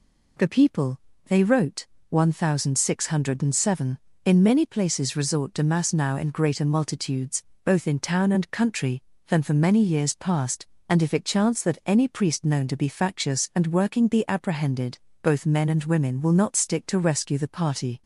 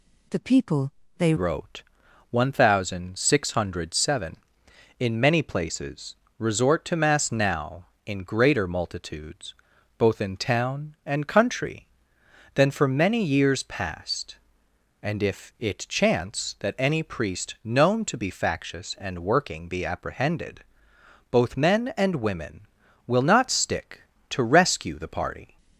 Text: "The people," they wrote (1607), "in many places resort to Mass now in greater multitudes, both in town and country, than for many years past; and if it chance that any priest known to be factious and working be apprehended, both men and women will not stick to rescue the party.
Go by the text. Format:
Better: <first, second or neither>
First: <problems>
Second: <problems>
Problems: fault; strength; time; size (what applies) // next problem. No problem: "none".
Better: first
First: none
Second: changes voice at "wrote"; from 1.3 s on; 24.2 s long // pauses between "places" and "resort"; slight; at 6.1 s; 0.22 s long